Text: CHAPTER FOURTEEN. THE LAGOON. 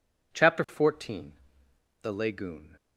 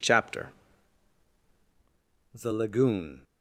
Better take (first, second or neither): first